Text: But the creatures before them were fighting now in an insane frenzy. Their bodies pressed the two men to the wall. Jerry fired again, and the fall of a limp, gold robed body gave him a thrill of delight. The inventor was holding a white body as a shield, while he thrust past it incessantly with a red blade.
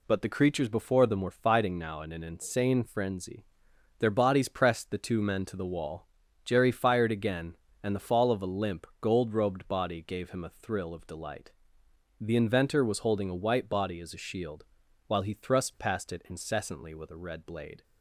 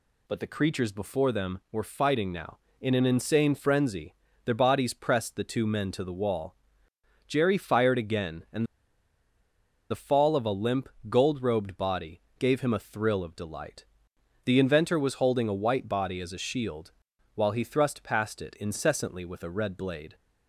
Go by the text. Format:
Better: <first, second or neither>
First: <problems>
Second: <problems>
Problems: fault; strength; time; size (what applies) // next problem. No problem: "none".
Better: first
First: none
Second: pauses between "and" and "the"; strong; at 8.6 s; 1.2 s long // pauses between "body" and "gave"; slight; at 12.2 s; 0.18 s long